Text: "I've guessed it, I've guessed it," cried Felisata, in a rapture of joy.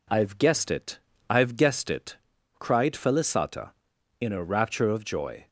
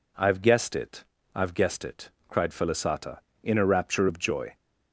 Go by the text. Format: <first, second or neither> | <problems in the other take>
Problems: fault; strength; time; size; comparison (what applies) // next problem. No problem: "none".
neither | none